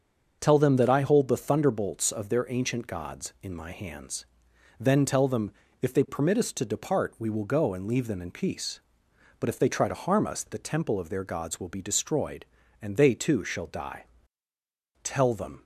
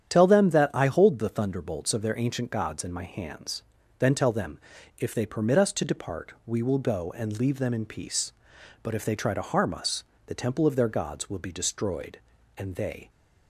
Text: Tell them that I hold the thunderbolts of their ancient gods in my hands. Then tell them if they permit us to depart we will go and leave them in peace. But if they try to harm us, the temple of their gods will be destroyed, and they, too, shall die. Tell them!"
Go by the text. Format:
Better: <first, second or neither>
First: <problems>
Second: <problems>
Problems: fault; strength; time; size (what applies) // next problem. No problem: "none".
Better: first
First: starts louder than the rest; until 1.4 s; 6.5 dB // pauses between "them" and "if"; slight; at 5.5 s; 0.30 s long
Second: starts louder than the rest; strong; until 1.1 s; 9 dB // pauses between "them" and "if"; at 4.5 s; 0.40 s long // stops before "too shall die Tell them"; at 13.0 s